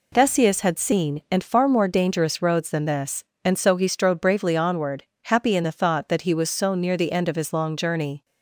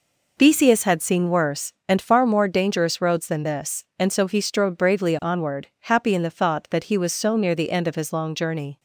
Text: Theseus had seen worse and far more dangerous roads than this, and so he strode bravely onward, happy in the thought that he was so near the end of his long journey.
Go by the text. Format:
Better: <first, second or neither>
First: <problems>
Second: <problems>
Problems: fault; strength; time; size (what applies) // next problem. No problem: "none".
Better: second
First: skips "worse"; at 1.2 s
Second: none